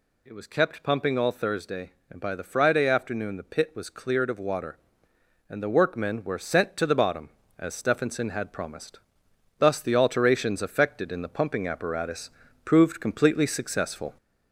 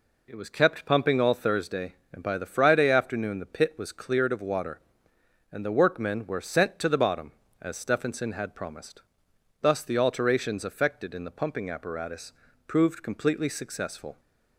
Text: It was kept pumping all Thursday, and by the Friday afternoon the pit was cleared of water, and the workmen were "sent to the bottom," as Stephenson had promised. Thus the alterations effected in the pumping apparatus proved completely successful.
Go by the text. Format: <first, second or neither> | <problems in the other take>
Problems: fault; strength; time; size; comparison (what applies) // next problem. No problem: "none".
second | gets louder; throughout; 3.5 dB // pauses between "apparatus" and "proved"; slight; at 12.2 s; 0.36 s long; slight in the second